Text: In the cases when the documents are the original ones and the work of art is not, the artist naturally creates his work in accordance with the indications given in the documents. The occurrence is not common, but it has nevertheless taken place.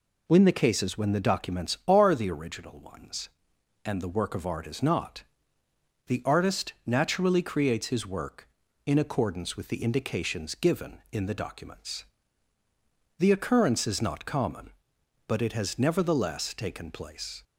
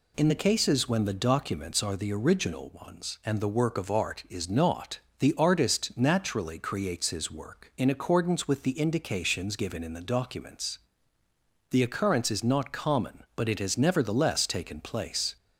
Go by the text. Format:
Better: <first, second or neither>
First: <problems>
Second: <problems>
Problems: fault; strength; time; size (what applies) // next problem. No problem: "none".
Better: neither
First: none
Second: none